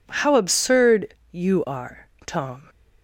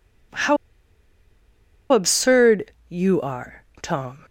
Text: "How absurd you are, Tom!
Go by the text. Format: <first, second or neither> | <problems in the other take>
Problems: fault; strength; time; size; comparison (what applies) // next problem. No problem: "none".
first | pauses between "How" and "absurd"; strong; at 0.5 s; 1.3 s long // pauses between "absurd" and "you"; slight; at 2.7 s; 0.16 s long; slight in the first